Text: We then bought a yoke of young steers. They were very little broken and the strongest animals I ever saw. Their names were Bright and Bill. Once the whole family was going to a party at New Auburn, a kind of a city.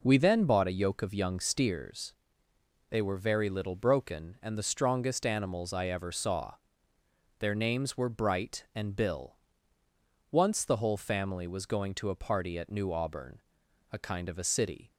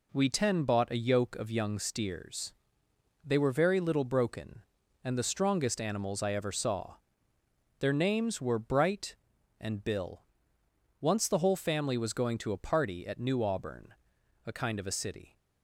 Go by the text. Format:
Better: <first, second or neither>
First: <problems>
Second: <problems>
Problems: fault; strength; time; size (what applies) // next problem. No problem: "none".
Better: first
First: none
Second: says "ten" for "then"; at 0.2 s